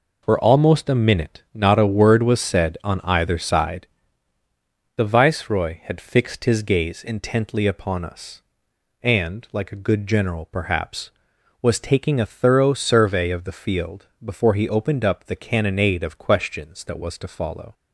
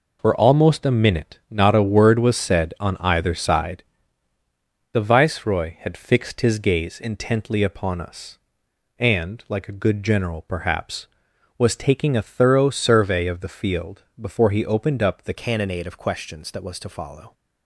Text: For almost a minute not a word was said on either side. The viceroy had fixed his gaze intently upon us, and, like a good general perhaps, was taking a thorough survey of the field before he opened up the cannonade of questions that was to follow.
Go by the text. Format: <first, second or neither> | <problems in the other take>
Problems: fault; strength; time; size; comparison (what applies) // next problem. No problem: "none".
first | pauses between "field" and "before"; slight; at 14.0 s; 0.16 s long; slight in the first // changes voice at "cannonade"; from 15.3 s on; 2.0 s long